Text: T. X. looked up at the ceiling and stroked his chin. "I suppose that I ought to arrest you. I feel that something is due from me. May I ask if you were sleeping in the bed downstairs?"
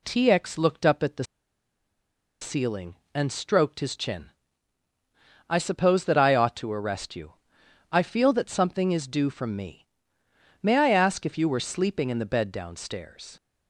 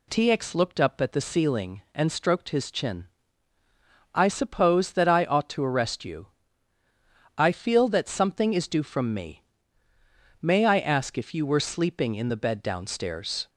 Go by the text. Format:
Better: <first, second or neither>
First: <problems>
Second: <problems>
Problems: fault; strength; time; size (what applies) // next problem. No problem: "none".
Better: second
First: pauses between "the" and "ceiling"; at 1.2 s; 1.1 s long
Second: none